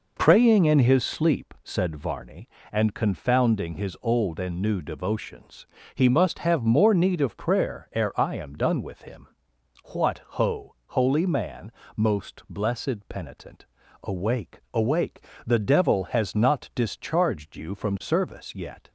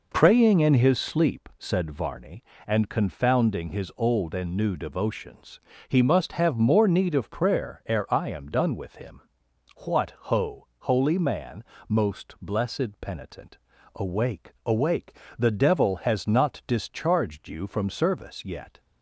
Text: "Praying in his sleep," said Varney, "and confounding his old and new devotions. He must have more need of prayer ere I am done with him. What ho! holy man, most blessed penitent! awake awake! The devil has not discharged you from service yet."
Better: neither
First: none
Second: none

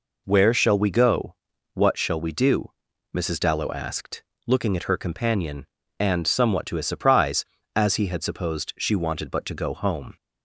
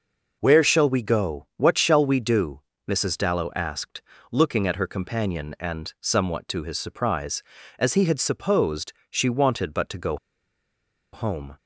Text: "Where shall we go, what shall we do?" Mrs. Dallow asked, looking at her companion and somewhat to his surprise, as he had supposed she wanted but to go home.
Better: first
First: none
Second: pauses between "supposed" and "she"; slight; at 8.9 s; 0.18 s long // pauses between "go" and "home"; noticeable; at 10.1 s; 0.96 s long

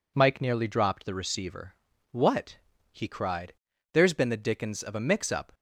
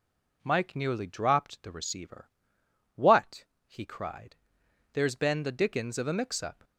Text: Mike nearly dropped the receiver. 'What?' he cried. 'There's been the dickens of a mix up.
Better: neither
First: none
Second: none

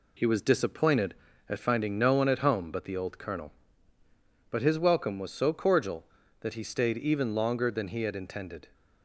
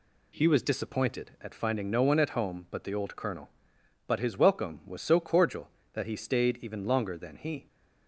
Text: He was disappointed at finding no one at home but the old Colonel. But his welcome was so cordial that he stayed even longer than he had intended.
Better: first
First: none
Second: stops before "had intended"; at 7.6 s

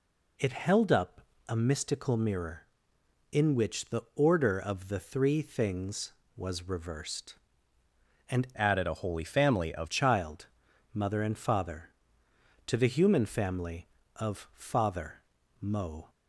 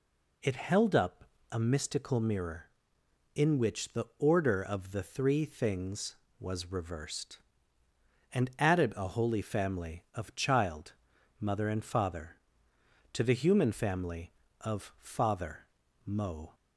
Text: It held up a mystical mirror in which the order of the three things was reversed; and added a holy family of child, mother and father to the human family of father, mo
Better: second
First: pauses between "up" and "a"; slight; at 1.2 s; 0.26 s long // changes voice from "added" to "of"; from 8.5 to 9.9 s; 1.4 s long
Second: pauses between "up" and "a"; slight; at 1.2 s; 0.26 s long

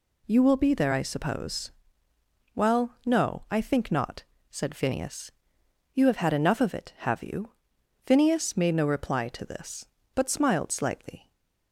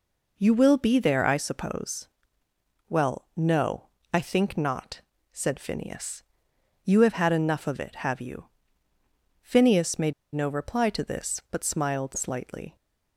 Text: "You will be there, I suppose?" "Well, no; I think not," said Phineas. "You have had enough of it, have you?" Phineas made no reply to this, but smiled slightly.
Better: first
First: none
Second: pauses between "made" and "no"; slight; at 10.1 s; 0.21 s long

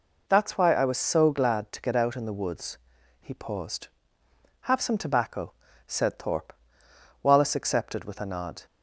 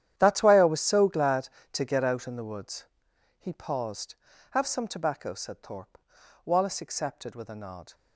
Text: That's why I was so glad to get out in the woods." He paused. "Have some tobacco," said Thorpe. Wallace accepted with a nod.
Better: first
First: none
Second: gets quieter; strong; throughout; 17 dB

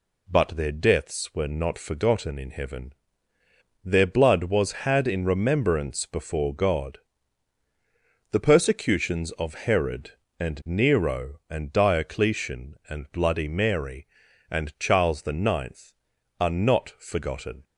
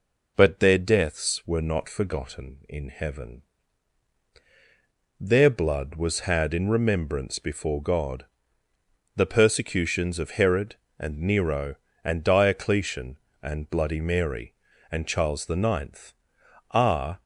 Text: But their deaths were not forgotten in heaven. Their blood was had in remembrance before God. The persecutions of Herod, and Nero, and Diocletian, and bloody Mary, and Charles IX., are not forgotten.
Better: first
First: none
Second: stops before "not forgotten"; at 17.2 s

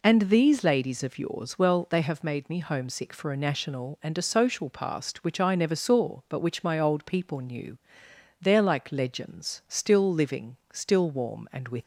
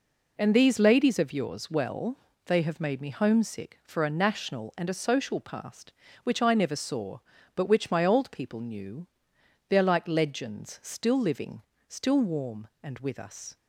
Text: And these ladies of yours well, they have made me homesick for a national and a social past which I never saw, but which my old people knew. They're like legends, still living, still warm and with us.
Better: second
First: stops before "us"; at 11.8 s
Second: none

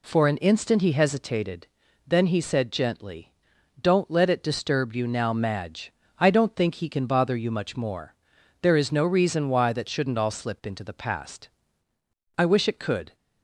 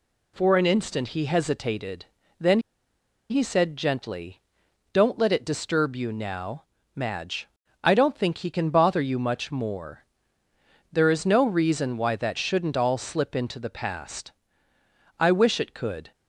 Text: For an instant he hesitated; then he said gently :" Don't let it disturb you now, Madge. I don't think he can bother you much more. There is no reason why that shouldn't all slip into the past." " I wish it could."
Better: first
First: none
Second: pauses between "then" and "he"; noticeable; at 2.5 s; 0.71 s long

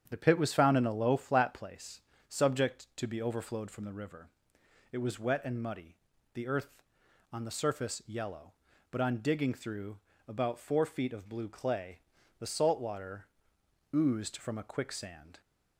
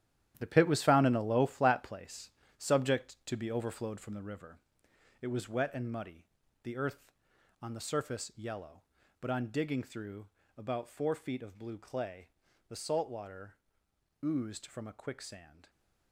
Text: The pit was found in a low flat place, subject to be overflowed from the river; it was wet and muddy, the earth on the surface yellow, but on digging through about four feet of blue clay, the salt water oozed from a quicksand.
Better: first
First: starts louder than the rest; strong; until 1.0 s; 8.5 dB // pauses between "through" and "about"; slight; at 9.9 s; 0.32 s long // pauses between "water" and "oozed"; noticeable; at 13.2 s; 0.66 s long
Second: gets quieter; strong; throughout; 10.5 dB // starts louder than the rest; strong; until 1.3 s; 11.5 dB // pauses between "through" and "about"; slight; at 10.2 s; 0.32 s long // pauses between "water" and "oozed"; noticeable; at 13.5 s; 0.66 s long

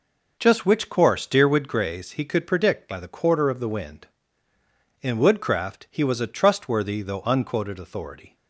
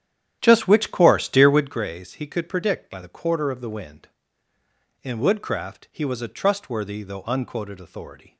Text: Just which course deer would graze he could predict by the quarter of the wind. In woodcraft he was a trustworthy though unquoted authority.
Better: first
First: none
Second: starts louder than the rest; strong; until 1.8 s; 10.5 dB

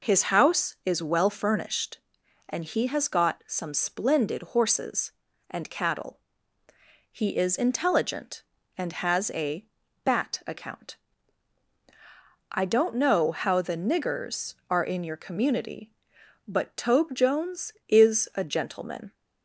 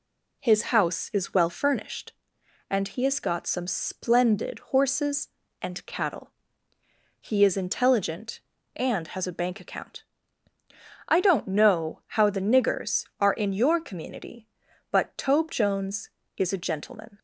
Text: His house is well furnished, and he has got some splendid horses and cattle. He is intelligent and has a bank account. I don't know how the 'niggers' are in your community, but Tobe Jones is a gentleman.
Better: second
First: says "bat" for "bank"; at 10.0 s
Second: none

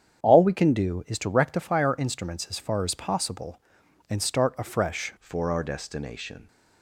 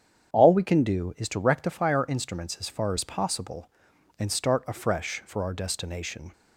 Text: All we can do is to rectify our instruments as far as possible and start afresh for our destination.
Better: second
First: starts louder than the rest; strong; until 1.2 s; 8.5 dB // changes voice at "for"; from 5.1 s on; 1.3 s long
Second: starts louder than the rest; strong; until 1.3 s; 8 dB

